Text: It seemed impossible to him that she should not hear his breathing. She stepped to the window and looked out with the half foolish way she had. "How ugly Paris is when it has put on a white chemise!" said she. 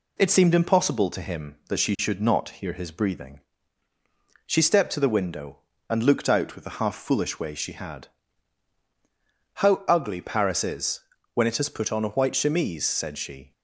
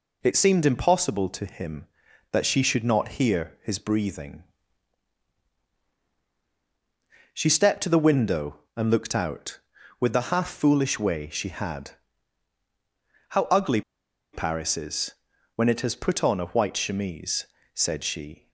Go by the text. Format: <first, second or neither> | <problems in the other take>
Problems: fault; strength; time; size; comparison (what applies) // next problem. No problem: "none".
first | pauses between "ugly" and "Paris"; noticeable; at 13.8 s; 0.52 s long // pauses between "is" and "when"; at 15.1 s; 0.44 s long; slight in the first